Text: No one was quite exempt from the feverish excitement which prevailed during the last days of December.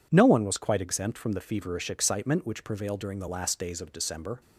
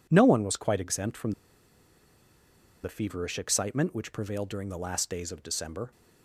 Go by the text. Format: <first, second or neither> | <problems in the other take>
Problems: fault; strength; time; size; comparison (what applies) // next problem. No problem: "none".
first | pauses between "from" and "the"; strong; at 1.3 s; 1.5 s long